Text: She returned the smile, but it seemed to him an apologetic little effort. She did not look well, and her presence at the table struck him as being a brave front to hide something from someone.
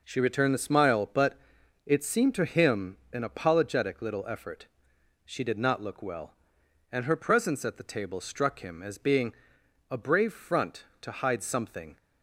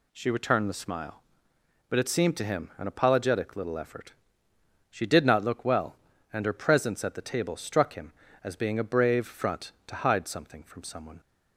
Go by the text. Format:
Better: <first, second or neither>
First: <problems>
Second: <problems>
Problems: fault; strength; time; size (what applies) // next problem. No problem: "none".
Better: second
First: pauses between "but" and "it"; noticeable; at 1.3 s; 0.50 s long // pauses between "him" and "an"; slight; at 2.9 s; 0.16 s long // pauses between "being" and "a"; noticeable; at 9.3 s; 0.56 s long // stops before "from someone"; at 11.9 s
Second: none